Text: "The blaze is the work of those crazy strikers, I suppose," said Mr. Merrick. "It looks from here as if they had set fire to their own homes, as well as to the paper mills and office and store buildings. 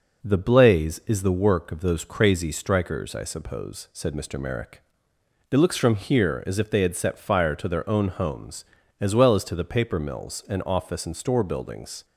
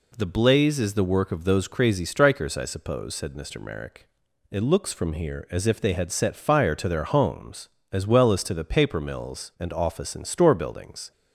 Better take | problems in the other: first | skips "own"; at 7.0 s

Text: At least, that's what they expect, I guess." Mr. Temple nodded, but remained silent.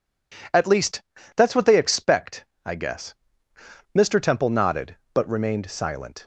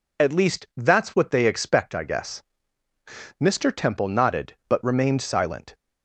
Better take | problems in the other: neither | none

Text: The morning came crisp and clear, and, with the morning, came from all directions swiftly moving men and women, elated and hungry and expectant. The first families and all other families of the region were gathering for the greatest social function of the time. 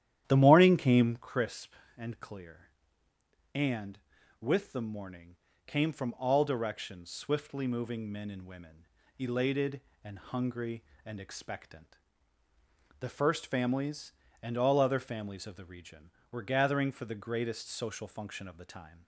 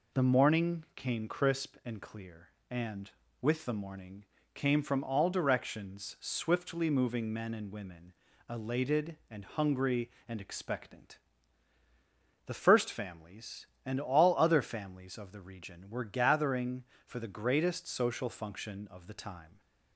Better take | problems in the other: second | starts louder than the rest; strong; until 1.3 s; 11 dB

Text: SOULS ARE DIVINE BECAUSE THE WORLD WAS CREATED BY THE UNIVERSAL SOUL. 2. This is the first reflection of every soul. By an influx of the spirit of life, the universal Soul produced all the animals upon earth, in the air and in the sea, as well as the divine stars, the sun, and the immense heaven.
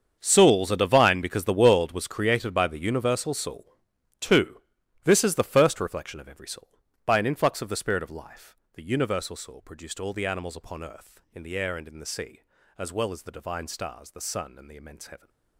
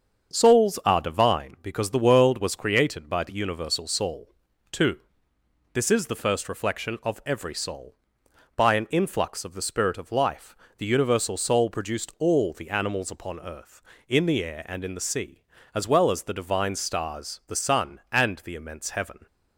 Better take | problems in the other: second | gets quieter; strong; throughout; 16 dB // starts louder than the rest; until 1.2 s; 7 dB; also in the second

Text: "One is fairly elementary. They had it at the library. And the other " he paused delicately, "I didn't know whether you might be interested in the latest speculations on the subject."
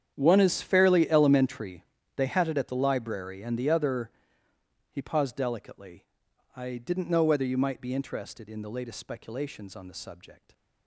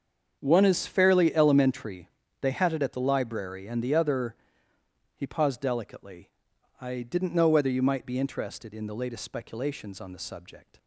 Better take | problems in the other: second | gets quieter; strong; throughout; 16 dB // starts louder than the rest; strong; until 1.1 s; 8.5 dB; also in the second

